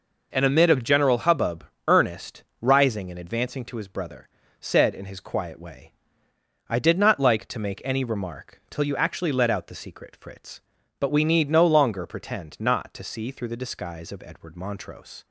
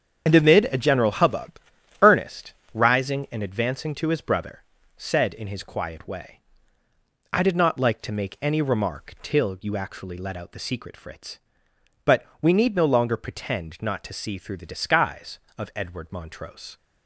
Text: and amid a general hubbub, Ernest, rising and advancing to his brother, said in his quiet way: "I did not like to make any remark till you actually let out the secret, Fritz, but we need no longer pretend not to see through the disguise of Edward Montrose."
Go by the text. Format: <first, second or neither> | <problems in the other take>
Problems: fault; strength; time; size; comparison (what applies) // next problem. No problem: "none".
first | loses the start of "and"; at 0.2 s; 50 ms // starts louder than the rest; strong; until 1.2 s; 8 dB // pauses between "but" and "we"; slight; at 12.2 s; 0.16 s long